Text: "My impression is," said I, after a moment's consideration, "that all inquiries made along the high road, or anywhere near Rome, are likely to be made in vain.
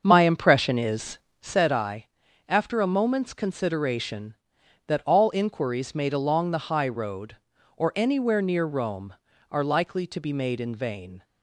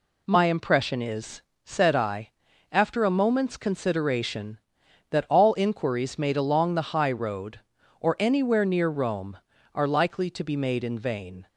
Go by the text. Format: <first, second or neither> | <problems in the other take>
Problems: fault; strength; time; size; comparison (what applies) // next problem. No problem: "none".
second | starts louder than the rest; until 1.6 s; 6.5 dB